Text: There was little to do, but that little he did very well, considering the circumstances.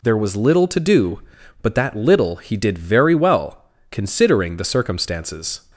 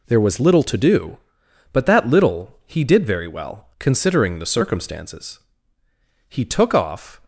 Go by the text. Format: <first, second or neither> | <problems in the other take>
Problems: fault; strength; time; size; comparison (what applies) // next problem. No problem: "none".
first | goes on to say "He took off"; noticeable; from 6.2 s on; 0.94 s long